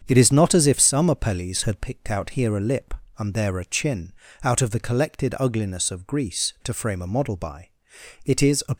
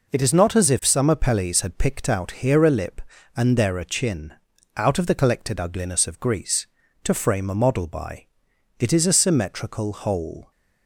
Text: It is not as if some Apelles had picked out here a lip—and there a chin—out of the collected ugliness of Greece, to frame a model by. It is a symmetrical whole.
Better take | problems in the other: second | starts louder than the rest; strong; until 1.0 s; 7.5 dB // stops before "symmetrical whole"; at 8.7 s

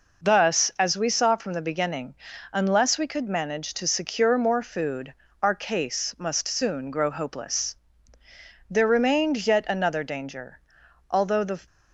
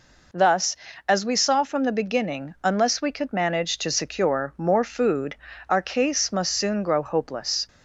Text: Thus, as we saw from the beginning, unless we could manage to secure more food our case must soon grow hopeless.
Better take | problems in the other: second | pauses between "food" and "our"; slight; at 5.1 s; 0.28 s long; slight in the second // goes on to say "There remained yet another danger Although the"; strong; from 8.6 s on; 2.9 s long

